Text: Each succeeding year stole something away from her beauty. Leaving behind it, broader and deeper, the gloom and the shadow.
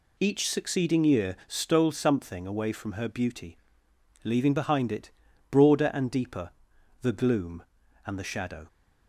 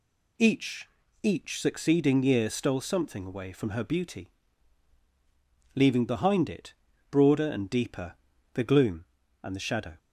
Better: first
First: none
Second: says "Each" twice; at 1.2 s

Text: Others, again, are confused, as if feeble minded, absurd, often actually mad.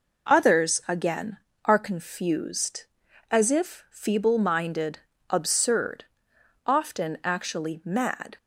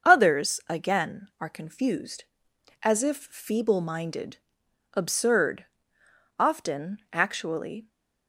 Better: first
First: none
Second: starts louder than the rest; until 1.1 s; 6.5 dB // stops before "mad"; at 7.9 s

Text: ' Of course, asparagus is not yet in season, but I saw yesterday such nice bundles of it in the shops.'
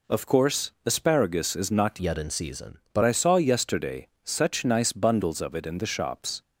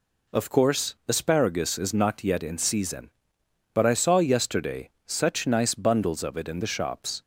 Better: second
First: changes voice from "yet" to "but"; from 2.0 to 3.0 s; 1.0 s long // pauses between "yesterday" and "such"; slight; at 4.0 s; 0.16 s long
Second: pauses between "yesterday" and "such"; slight; at 4.8 s; 0.16 s long

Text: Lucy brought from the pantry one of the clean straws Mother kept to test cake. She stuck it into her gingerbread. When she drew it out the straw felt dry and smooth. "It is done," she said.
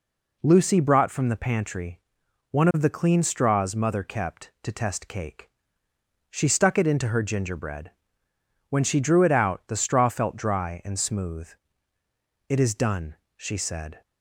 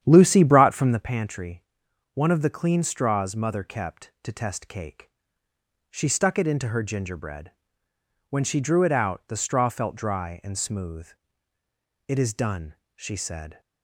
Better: first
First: pauses between "pantry" and "one"; noticeable; at 1.9 s; 0.54 s long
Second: starts louder than the rest; strong; until 1.0 s; 9.5 dB // pauses between "pantry" and "one"; noticeable; at 1.6 s; 0.54 s long

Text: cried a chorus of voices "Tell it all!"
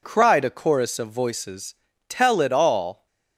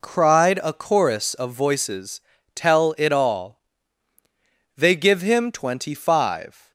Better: first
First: pauses between "voices" and "Tell"; slight; at 1.7 s; 0.36 s long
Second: pauses between "voices" and "Tell"; slight; at 2.2 s; 0.34 s long // goes on to say "They give him twenty five"; strong; from 4.7 s on; 1.9 s long

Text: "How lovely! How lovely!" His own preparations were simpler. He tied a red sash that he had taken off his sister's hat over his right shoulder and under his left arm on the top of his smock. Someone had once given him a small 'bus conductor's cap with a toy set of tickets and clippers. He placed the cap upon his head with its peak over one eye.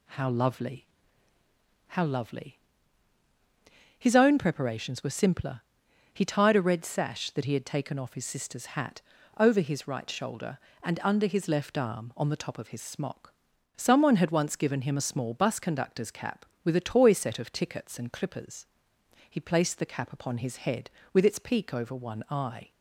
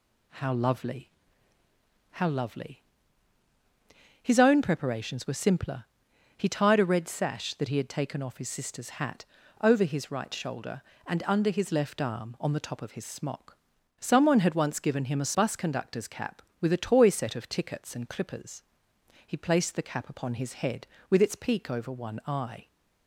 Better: first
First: pauses between "hat" and "over"; at 9.0 s; 0.38 s long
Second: pauses between "hat" and "over"; at 9.2 s; 0.38 s long // skips "small"; at 15.3 s

